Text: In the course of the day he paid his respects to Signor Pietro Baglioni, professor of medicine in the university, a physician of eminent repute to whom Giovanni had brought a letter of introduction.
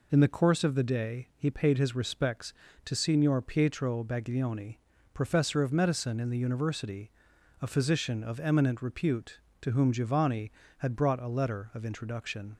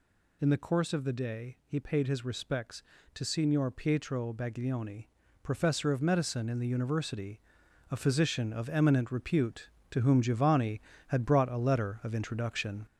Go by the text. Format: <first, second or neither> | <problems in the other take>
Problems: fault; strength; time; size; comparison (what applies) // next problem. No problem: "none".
first | gets louder; noticeable; throughout; 4.5 dB